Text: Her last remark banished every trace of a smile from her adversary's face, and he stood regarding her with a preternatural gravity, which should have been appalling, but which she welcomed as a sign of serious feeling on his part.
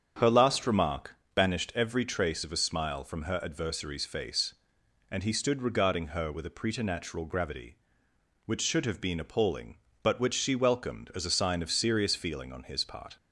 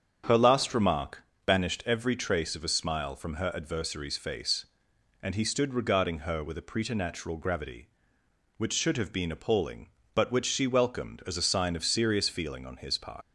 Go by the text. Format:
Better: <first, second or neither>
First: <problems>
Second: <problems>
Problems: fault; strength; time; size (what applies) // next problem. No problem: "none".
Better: first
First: starts louder than the rest; strong; until 1.3 s; 7.5 dB // pauses between "remark" and "banished"; slight; at 1.1 s; 0.20 s long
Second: starts louder than the rest; strong; until 1.5 s; 7.5 dB // pauses between "remark" and "banished"; slight; at 1.2 s; 0.23 s long // leaves "part" unfinished; at 13.2 s; 85 ms